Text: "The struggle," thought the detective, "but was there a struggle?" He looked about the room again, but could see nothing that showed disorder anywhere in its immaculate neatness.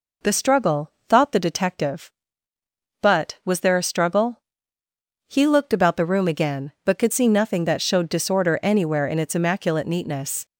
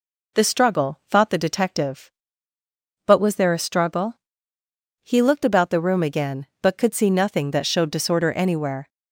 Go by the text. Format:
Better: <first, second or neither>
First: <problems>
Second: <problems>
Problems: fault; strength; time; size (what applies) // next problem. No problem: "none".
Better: first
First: none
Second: stops before "in its immaculate neatness"; at 8.8 s